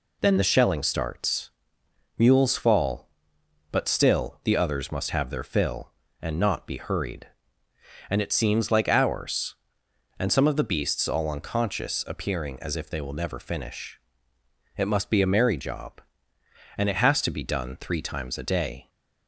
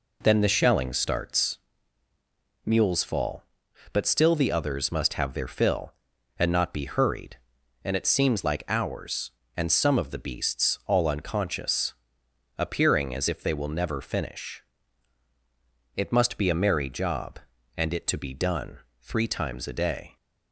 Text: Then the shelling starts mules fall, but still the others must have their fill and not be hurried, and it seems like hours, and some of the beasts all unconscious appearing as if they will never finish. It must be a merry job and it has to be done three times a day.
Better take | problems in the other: first | pauses between "starts" and "mules"; at 1.5 s; 1.0 s long; noticeable in the first // pauses between "unconscious" and "appearing"; noticeable; at 11.9 s; 0.64 s long // skips "has"; at 18.0 s // pauses between "done" and "three"; slight; at 18.7 s; 0.22 s long

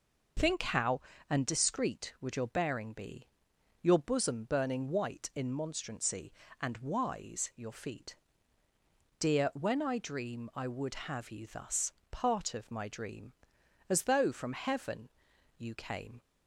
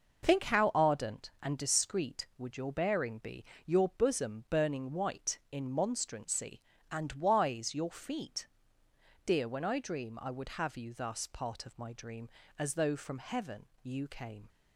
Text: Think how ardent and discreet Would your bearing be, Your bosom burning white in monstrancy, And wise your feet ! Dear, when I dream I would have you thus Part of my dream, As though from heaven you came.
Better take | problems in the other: second | skips "ardent"; at 1.1 s // pauses between "thus" and "Part"; slight; at 11.9 s; 0.20 s long // pauses between "heaven" and "you"; noticeable; at 15.0 s; 0.50 s long; slight in the second

